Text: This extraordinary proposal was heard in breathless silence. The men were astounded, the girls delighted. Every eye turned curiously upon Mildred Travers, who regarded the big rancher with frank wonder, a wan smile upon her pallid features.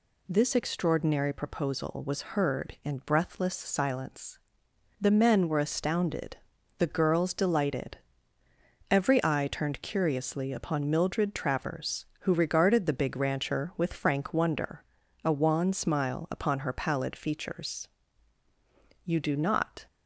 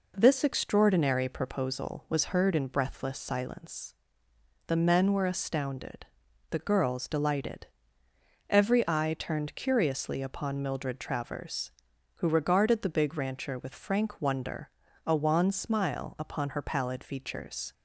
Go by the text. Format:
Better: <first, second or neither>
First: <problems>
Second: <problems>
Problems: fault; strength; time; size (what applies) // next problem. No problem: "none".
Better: second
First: goes on to say "You do not"; noticeable; from 19.0 s on; 0.82 s long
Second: none